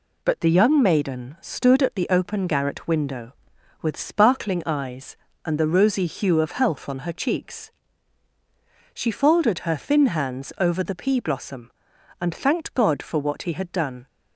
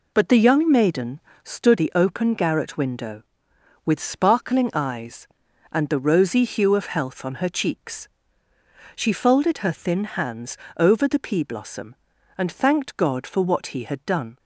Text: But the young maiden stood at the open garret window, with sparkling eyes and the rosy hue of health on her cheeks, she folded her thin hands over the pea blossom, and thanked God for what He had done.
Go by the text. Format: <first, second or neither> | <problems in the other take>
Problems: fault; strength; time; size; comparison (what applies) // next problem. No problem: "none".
first | pauses between "maiden" and "stood"; slight; at 1.2 s; 0.22 s long // skips "at"; at 1.7 s // pauses between "hands" and "over"; slight; at 10.5 s; 0.20 s long